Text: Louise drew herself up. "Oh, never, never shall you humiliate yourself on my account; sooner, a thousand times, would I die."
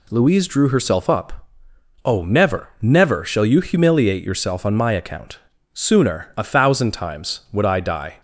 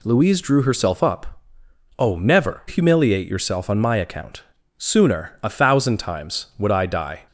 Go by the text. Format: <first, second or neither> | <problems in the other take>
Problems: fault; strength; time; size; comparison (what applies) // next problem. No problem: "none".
first | skips "never shall you"; at 2.6 s